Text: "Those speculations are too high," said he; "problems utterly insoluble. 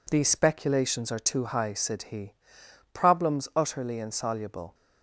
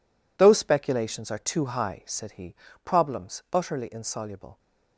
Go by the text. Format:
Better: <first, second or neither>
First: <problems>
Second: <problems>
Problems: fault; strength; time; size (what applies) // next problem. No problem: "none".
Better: second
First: says "These" for "Those"; at 0.0 s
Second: none